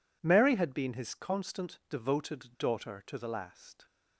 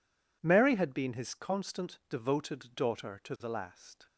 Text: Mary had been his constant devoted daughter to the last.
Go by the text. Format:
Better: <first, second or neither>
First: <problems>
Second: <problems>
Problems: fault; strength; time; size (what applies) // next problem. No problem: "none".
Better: neither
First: none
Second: none